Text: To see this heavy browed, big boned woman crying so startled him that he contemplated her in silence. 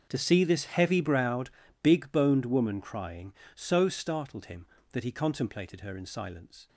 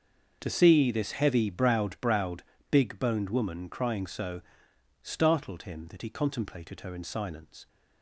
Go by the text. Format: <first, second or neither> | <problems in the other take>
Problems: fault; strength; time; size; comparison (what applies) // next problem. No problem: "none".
first | starts louder than the rest; until 1.4 s; 6.5 dB; noticeable in the first // says "browed" twice; at 1.9 s // pauses between "so" and "startled"; noticeable; at 4.4 s; 0.60 s long